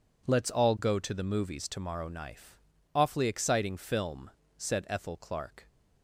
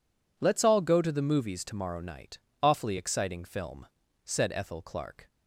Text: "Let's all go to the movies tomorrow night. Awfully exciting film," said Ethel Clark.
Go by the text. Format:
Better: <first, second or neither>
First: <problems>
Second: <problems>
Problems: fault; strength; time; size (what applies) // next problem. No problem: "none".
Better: second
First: says "knife" for "night"; at 2.0 s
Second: none